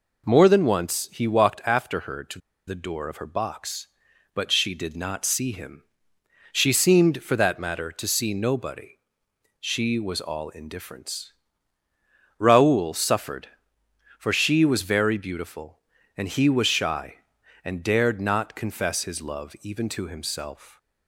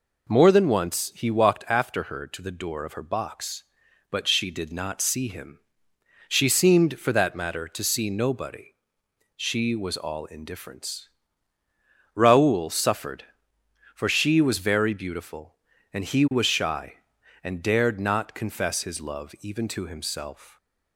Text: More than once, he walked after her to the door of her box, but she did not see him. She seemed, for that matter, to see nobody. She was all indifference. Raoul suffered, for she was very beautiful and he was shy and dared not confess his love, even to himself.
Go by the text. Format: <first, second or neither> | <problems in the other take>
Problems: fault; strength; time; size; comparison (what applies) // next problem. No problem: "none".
second | pauses between "to" and "the"; slight; at 2.3 s; 0.28 s long